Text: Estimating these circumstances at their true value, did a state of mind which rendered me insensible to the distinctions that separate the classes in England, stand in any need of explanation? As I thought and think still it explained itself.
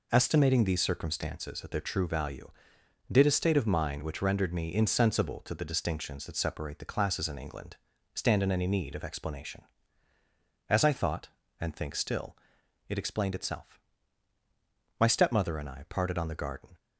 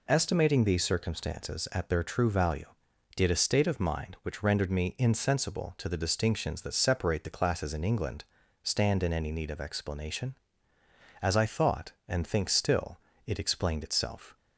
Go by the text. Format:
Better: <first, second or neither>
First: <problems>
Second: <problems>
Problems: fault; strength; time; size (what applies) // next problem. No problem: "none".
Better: second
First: pauses between "still" and "it"; noticeable; at 12.3 s; 0.52 s long // goes on to say "My stepmother and I parted on the garden"; strong; from 14.9 s on; 1.8 s long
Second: pauses between "still" and "it"; slight; at 12.9 s; 0.28 s long